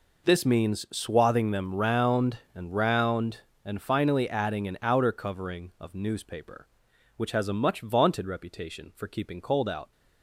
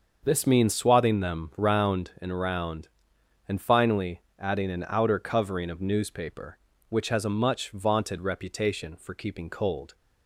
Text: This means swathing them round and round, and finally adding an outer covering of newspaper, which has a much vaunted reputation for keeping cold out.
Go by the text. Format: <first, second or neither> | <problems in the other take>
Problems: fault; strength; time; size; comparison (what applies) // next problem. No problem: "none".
first | starts louder than the rest; until 1.2 s; 6.5 dB // pauses between "finally" and "adding"; slight; at 4.2 s; 0.18 s long // stops before "out"; at 9.9 s